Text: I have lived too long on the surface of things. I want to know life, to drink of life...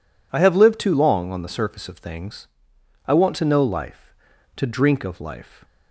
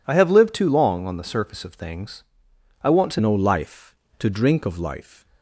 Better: first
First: none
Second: changes voice at "know"; from 3.1 s on; 2.1 s long

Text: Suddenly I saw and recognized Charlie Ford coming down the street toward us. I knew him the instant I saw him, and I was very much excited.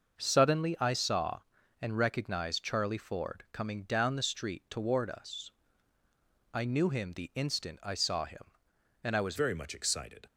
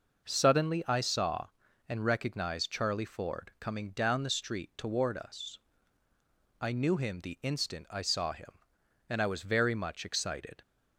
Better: second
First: starts louder than the rest; until 1.2 s; 6 dB // changes voice at "very"; from 9.3 s on; 0.9 s long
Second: none

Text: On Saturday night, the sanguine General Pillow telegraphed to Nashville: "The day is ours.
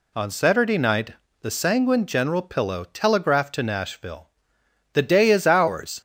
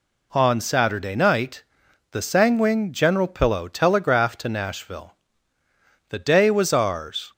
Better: first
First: none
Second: says "was" for "is"; at 6.5 s

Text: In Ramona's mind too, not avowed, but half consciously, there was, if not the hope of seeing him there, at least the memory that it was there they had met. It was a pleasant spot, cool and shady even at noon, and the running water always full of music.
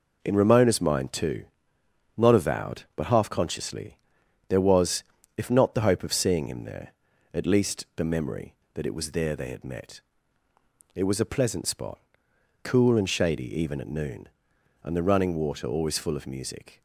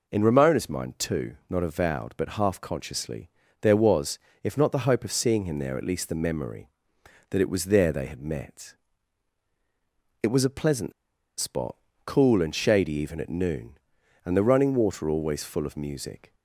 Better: first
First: none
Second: pauses between "pleasant" and "spot"; noticeable; at 10.9 s; 0.47 s long

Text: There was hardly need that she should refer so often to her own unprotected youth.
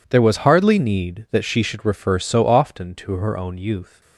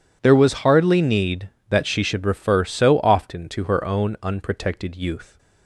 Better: second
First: skips "unprotected"; at 3.5 s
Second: none

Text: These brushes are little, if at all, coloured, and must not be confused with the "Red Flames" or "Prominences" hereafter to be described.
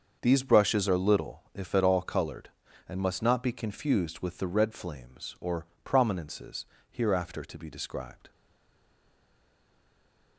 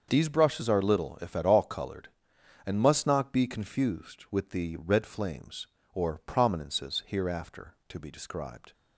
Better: second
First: starts louder than the rest; until 1.2 s; 6.5 dB // pauses between "or" and "Prominences"; slight; at 5.6 s; 0.16 s long // pauses between "Prominences" and "hereafter"; slight; at 6.6 s; 0.24 s long // stays silent after the last word; noticeable; from 8.3 s on; 2.0 s long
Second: starts louder than the rest; until 1.1 s; 6 dB

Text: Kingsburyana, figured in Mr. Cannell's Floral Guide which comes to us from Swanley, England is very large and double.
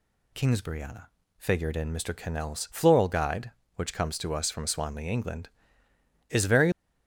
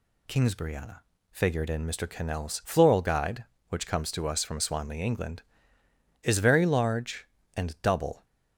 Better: second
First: stops before "large and double"; at 6.7 s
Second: none

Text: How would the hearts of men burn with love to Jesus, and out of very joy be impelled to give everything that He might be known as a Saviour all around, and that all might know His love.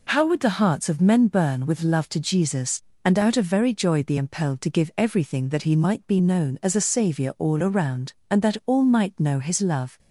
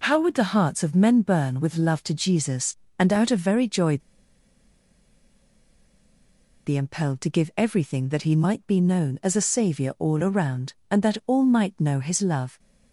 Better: first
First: none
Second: pauses between "joy" and "be"; strong; at 3.9 s; 2.6 s long

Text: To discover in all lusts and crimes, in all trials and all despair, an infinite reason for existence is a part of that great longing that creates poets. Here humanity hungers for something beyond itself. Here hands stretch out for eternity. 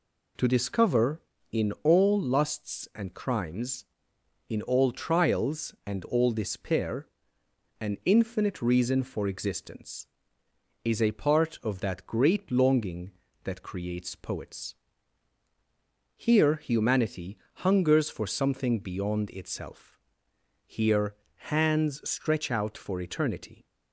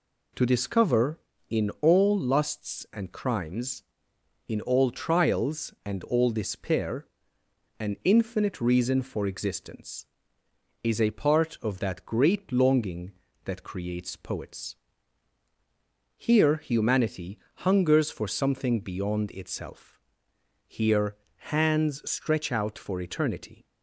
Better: neither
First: pauses between "humanity" and "hungers"; slight; at 17.3 s; 0.20 s long // pauses between "Here" and "hands"; slight; at 21.1 s; 0.36 s long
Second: pauses between "humanity" and "hungers"; slight; at 17.3 s; 0.20 s long // pauses between "Here" and "hands"; slight; at 21.1 s; 0.36 s long

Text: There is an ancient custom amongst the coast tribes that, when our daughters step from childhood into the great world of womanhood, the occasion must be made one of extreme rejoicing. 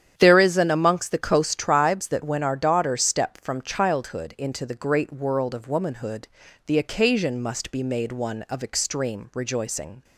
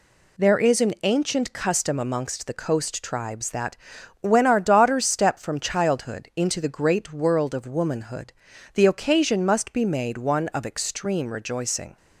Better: second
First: starts louder than the rest; strong; until 1.1 s; 9 dB // skips "ancient custom"; at 0.6 s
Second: none

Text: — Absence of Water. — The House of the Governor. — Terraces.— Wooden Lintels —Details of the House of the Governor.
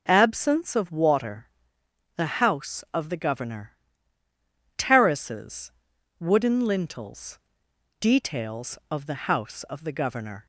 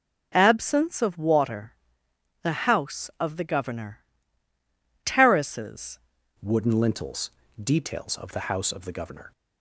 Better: first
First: none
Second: changes voice at "Wooden"; from 6.4 s on; 2.9 s long

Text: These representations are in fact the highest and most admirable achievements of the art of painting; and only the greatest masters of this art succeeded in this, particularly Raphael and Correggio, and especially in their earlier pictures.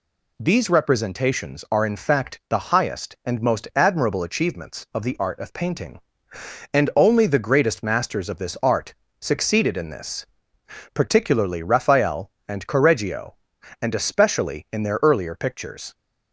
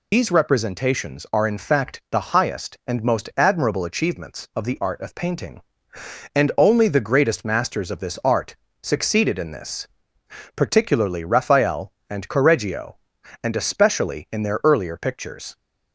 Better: first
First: pauses between "art" and "succeeded"; slight; at 8.9 s; 0.26 s long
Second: loses the start of "These"; at 0.1 s; 135 ms // pauses between "art" and "succeeded"; slight; at 8.5 s; 0.26 s long

